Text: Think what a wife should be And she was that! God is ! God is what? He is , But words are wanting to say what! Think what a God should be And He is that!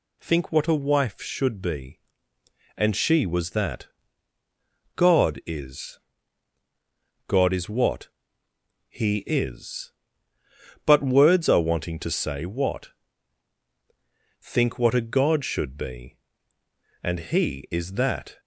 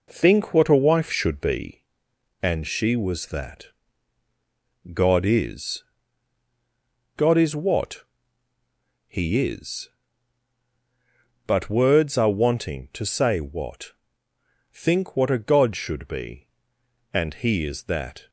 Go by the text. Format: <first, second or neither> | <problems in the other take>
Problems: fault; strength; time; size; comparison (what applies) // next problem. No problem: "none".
first | starts louder than the rest; noticeable; until 1.7 s; 4 dB